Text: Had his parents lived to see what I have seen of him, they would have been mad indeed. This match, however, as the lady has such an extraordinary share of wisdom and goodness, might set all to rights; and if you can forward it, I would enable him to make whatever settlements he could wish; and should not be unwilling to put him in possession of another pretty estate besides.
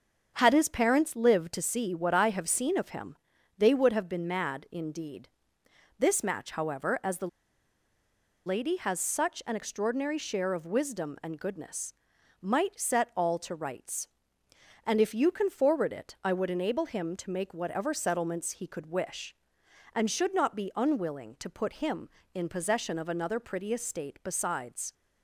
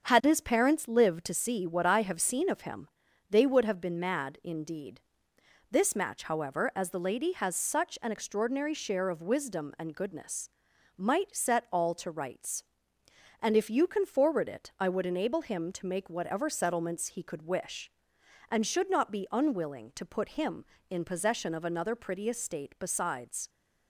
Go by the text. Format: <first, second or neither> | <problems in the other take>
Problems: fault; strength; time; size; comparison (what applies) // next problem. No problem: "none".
second | starts louder than the rest; until 1.3 s; 7 dB; also in the second // pauses between "the" and "lady"; at 7.2 s; 1.1 s long